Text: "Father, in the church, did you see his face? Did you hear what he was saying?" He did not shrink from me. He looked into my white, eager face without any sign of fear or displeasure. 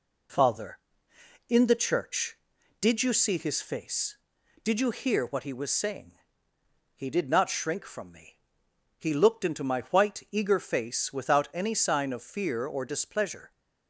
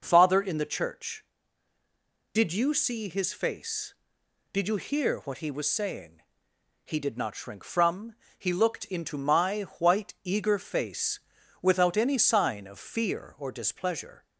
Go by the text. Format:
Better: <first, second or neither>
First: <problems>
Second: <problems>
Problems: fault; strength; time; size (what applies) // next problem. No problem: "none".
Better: first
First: none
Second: skips "me"; at 8.2 s // pauses between "my" and "white"; slight; at 9.6 s; 0.18 s long // pauses between "face" and "without"; at 11.1 s; 0.42 s long